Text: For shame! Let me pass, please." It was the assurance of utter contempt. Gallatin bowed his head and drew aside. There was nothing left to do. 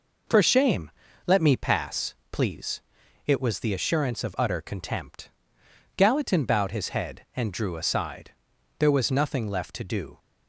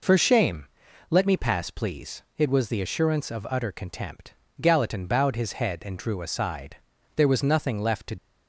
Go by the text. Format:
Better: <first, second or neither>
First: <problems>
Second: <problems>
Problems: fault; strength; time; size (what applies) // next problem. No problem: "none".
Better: first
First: none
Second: stops before "do"; at 8.1 s